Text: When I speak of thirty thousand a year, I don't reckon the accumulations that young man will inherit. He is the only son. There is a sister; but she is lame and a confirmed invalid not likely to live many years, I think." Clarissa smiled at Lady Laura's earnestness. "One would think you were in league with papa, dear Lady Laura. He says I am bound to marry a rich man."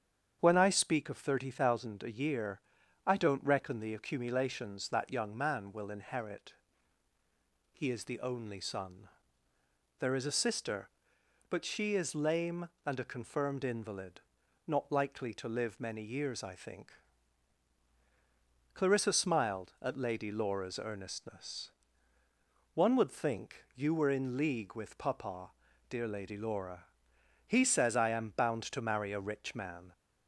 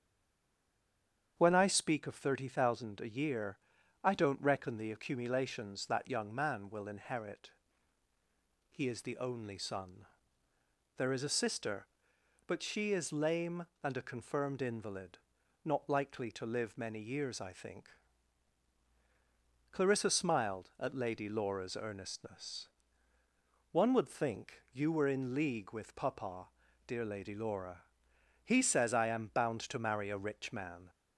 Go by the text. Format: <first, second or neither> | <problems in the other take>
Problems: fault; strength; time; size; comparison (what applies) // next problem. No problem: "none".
first | stays silent before the first word; noticeable; until 1.3 s; 1.3 s long // starts louder than the rest; strong; until 2.3 s; 8 dB; strong in the first // pauses between "invalid" and "not"; noticeable; at 15.1 s; 0.46 s long; noticeable in the first